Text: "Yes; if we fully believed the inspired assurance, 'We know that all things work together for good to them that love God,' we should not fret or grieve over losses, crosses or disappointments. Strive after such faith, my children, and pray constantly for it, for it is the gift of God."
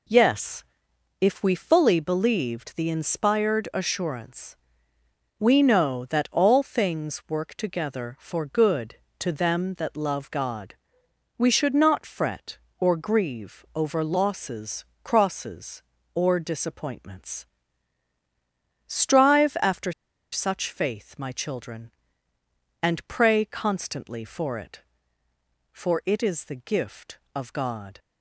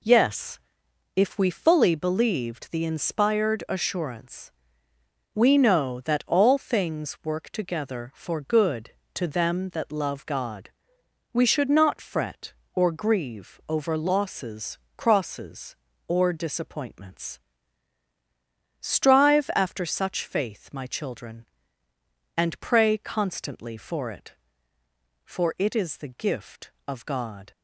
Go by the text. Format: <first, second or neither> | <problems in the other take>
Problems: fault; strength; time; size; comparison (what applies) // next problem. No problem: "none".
second | pauses between "after" and "such"; at 19.9 s; 0.40 s long